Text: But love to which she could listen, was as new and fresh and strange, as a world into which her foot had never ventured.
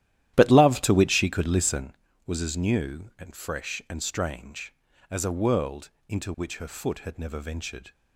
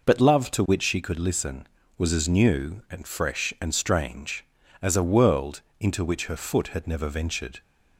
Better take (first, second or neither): second